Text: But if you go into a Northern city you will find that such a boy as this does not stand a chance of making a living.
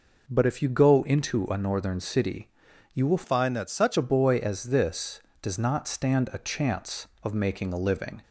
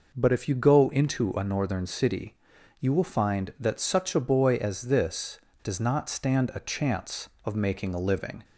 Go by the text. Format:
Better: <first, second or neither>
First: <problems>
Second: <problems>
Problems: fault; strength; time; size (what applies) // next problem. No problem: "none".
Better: second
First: pauses between "city" and "you"; at 2.5 s; 0.44 s long // changes voice from "find" to "such"; from 3.2 to 3.9 s; 0.7 s long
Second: pauses between "city" and "you"; at 2.3 s; 0.44 s long